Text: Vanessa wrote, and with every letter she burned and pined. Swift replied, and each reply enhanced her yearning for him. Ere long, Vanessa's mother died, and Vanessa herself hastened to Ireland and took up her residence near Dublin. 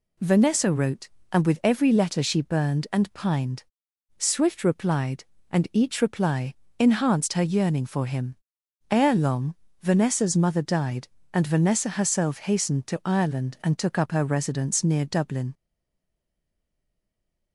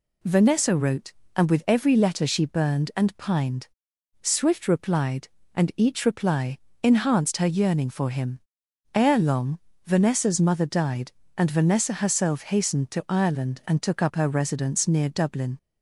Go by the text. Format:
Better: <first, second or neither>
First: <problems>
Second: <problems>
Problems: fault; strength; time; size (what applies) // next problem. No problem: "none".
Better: second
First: pauses between "reply" and "enhanced"; slight; at 6.5 s; 0.24 s long // stays silent after the last word; noticeable; from 15.5 s on; 2.0 s long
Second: pauses between "reply" and "enhanced"; slight; at 6.5 s; 0.24 s long